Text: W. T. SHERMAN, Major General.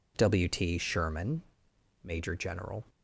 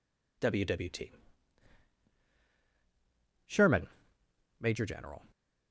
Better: first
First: none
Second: says "W" twice; at 0.6 s // pauses between "T" and "SHERMAN"; strong; at 1.1 s; 2.3 s long

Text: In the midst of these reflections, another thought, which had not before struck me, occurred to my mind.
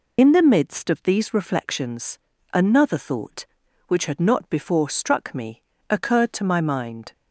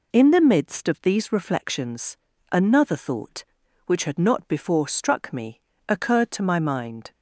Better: second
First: loses the start of "In"; at 0.1 s; 45 ms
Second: none

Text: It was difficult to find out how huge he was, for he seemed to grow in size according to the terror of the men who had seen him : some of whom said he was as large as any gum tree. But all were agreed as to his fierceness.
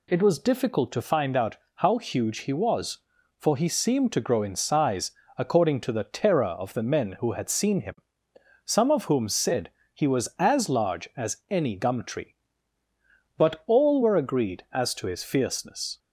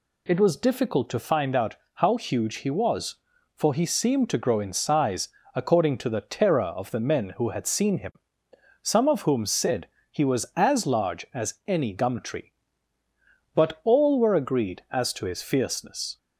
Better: neither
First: pauses between "out" and "how"; slight; at 1.5 s; 0.18 s long // pauses between "size" and "according"; slight; at 5.1 s; 0.24 s long // pauses between "said" and "he"; slight; at 9.6 s; 0.22 s long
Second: pauses between "out" and "how"; slight; at 1.7 s; 0.18 s long // pauses between "size" and "according"; slight; at 5.2 s; 0.24 s long // pauses between "said" and "he"; slight; at 9.8 s; 0.22 s long

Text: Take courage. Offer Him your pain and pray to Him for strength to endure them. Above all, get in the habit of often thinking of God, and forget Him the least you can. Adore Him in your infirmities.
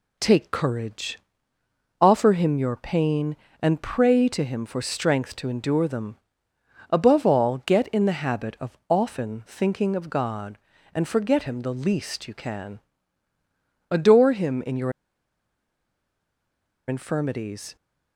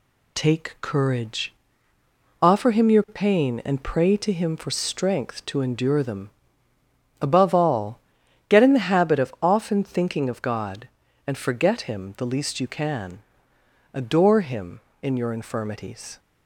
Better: second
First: pauses between "your" and "infirmities"; strong; at 14.9 s; 1.9 s long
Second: none

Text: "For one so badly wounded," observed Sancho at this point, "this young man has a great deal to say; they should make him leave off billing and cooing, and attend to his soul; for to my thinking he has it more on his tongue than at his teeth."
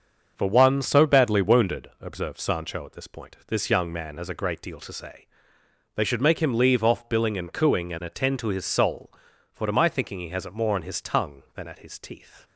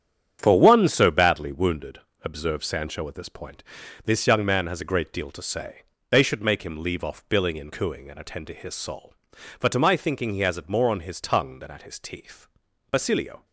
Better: first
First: starts louder than the rest; until 1.3 s; 6.5 dB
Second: starts louder than the rest; strong; until 1.4 s; 9 dB // goes on to say "Basilio"; from 12.9 s on; 0.54 s long

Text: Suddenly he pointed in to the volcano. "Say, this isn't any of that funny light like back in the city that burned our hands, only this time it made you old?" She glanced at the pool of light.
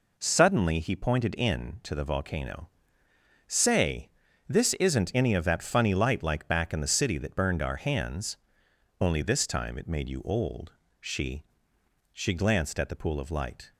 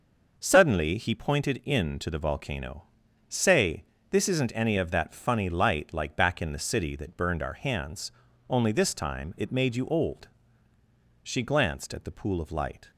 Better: second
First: says "She" twice; at 12.1 s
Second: none

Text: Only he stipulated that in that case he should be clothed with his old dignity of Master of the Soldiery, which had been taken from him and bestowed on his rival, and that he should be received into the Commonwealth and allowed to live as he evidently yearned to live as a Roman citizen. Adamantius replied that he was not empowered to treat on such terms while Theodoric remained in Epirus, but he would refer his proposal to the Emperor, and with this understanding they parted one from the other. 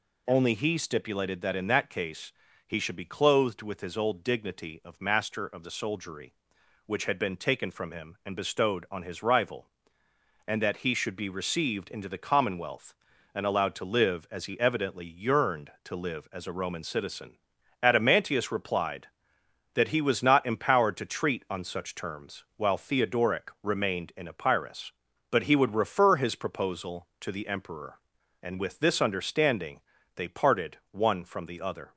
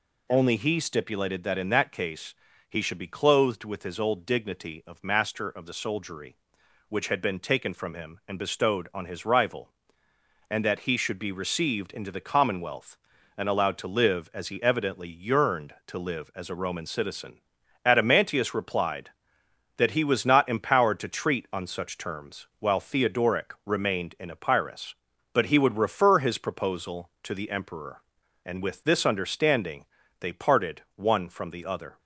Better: neither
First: pauses between "case" and "he"; slight; at 2.3 s; 0.36 s long // pauses between "understanding" and "they"; slight; at 29.8 s; 0.34 s long // pauses between "parted" and "one"; slight; at 30.7 s; 0.16 s long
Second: pauses between "case" and "he"; slight; at 2.3 s; 0.36 s long // pauses between "understanding" and "they"; slight; at 29.8 s; 0.34 s long // pauses between "parted" and "one"; slight; at 30.8 s; 0.16 s long

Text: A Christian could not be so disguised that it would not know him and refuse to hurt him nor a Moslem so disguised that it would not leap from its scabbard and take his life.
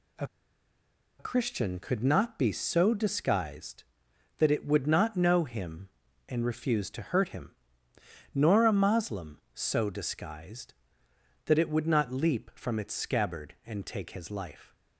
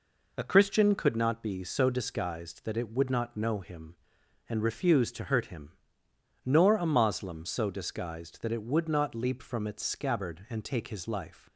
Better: second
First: pauses between "A" and "Christian"; noticeable; at 0.2 s; 0.93 s long // pauses between "him" and "nor"; noticeable; at 7.5 s; 0.84 s long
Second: pauses between "him" and "nor"; noticeable; at 5.7 s; 0.74 s long

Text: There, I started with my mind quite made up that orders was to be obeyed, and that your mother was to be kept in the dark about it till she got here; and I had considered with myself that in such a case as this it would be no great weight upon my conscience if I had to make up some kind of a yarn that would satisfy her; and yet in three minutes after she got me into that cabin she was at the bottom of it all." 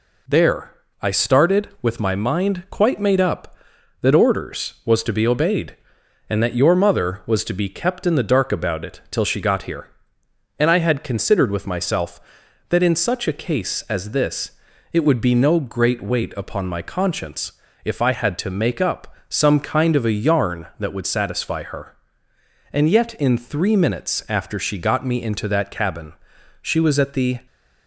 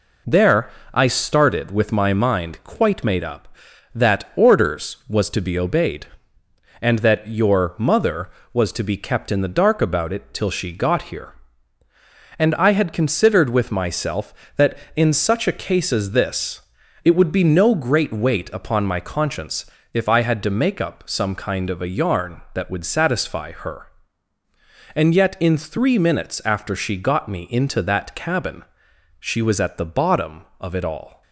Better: second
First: pauses between "this" and "it"; slight; at 14.5 s; 0.34 s long // pauses between "conscience" and "if"; slight; at 17.5 s; 0.32 s long // pauses between "up" and "some"; slight; at 19.1 s; 0.16 s long // pauses between "cabin" and "she"; noticeable; at 26.1 s; 0.50 s long // stops before "bottom of it all"; at 27.4 s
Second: pauses between "this" and "it"; at 16.6 s; 0.42 s long // pauses between "conscience" and "if"; slight; at 19.6 s; 0.26 s long // pauses between "cabin" and "she"; noticeable; at 28.6 s; 0.54 s long

